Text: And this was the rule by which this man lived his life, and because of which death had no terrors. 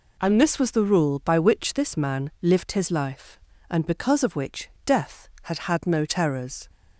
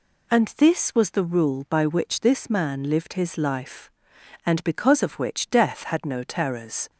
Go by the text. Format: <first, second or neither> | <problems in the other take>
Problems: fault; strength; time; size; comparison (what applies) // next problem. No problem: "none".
second | pauses between "which" and "death"; slight; at 4.6 s; 0.16 s long // says "had" twice; at 5.5 s